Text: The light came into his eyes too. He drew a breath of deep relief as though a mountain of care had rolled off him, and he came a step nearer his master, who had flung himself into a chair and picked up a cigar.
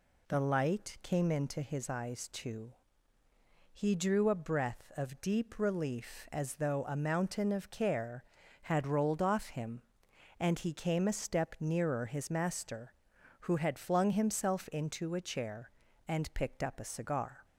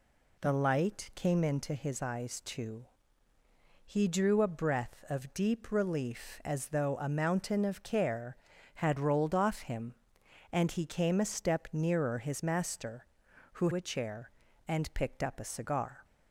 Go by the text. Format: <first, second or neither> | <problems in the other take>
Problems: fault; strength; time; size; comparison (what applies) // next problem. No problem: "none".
first | skips "had flung himself into"; at 13.7 s